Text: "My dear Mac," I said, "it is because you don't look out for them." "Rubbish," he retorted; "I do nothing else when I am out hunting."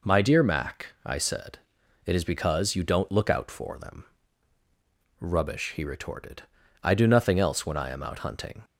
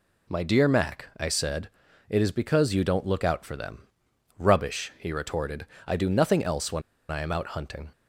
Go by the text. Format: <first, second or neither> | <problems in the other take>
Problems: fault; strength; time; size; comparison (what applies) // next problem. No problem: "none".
first | pauses between "when" and "I"; slight; at 6.8 s; 0.28 s long